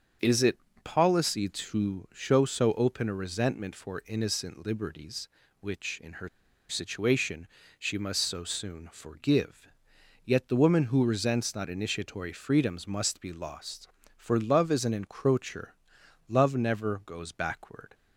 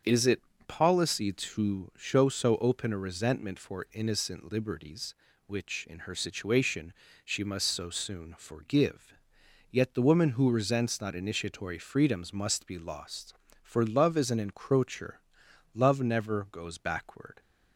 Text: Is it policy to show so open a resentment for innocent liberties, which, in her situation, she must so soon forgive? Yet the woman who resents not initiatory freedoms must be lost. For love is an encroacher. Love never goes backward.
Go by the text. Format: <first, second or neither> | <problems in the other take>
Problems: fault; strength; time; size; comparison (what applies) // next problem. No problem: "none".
second | starts louder than the rest; strong; until 1.4 s; 7 dB; strong in the second // pauses between "it" and "policy"; slight; at 0.5 s; 0.26 s long; slight in the second // pauses between "her" and "situation"; at 6.2 s; 0.40 s long